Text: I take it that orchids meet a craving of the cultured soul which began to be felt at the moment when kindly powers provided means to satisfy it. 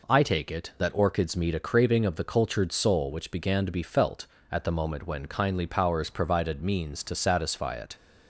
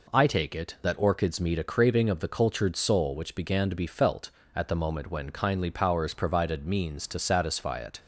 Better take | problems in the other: neither | none

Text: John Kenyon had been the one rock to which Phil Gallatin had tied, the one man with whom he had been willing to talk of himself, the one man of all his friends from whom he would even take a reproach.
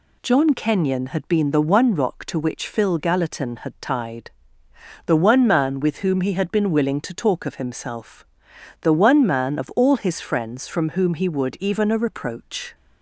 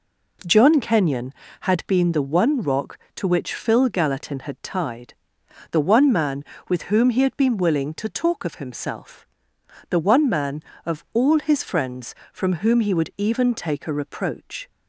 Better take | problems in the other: second | skips "take"; at 11.8 s

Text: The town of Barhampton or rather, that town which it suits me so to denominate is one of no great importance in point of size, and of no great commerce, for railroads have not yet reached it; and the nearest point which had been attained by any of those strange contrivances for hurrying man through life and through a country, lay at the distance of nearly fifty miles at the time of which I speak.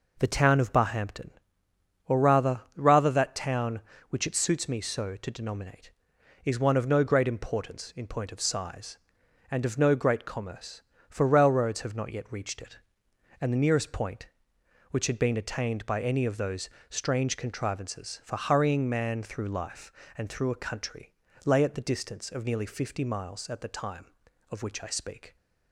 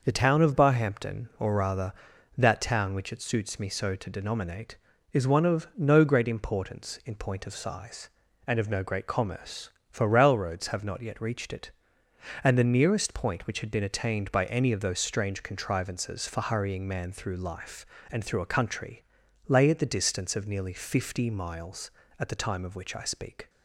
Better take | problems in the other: second | says "rather" twice; at 2.7 s // pauses between "those" and "strange"; slight; at 16.6 s; 0.22 s long

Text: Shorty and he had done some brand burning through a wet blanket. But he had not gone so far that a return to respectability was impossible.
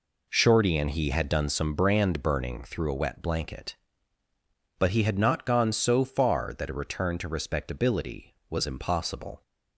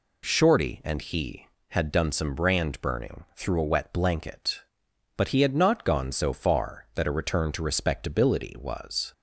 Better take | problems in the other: first | stops before "impossible"; at 9.1 s

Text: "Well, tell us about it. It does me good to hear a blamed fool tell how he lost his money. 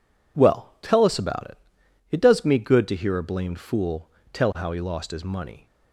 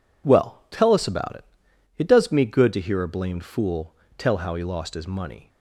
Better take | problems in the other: neither | pauses between "fool" and "tell"; slight; the same in both

